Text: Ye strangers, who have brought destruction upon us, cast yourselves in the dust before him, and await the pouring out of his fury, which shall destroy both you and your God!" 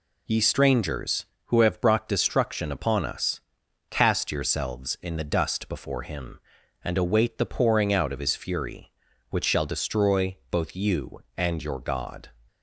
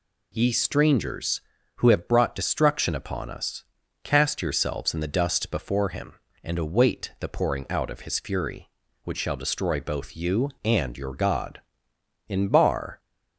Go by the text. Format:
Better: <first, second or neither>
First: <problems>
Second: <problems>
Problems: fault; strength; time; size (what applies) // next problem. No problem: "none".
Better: first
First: none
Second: goes on to say "In Bar"; noticeable; from 12.2 s on; 0.72 s long